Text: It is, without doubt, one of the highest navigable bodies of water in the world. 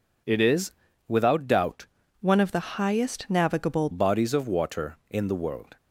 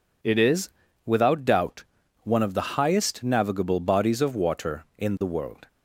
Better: second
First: changes voice from "one" to "navigable"; from 2.2 to 3.8 s; 1.6 s long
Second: none

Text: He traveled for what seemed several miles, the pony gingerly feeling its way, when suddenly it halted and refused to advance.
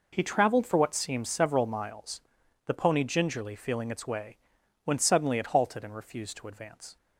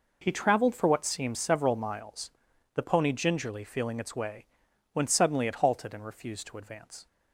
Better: neither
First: none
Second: none

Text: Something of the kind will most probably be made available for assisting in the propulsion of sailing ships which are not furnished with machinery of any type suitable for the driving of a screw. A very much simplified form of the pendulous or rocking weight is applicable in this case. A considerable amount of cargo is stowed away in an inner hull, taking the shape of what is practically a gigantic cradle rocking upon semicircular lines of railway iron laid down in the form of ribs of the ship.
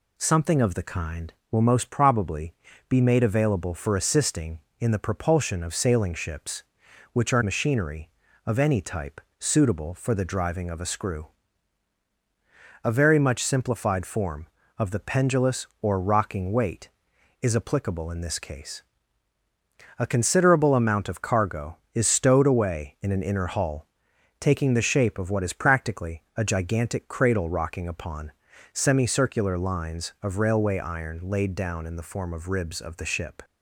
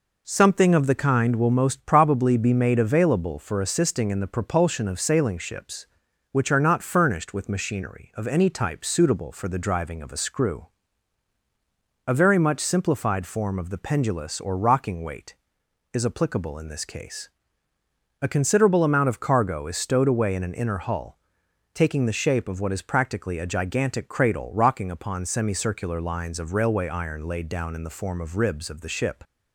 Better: second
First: pauses between "probably" and "be"; slight; at 2.5 s; 0.34 s long // skips "not furnished with"; at 7.4 s // pauses between "type" and "suitable"; slight; at 9.2 s; 0.18 s long // pauses between "upon" and "semicircular"; at 28.3 s; 0.42 s long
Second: none

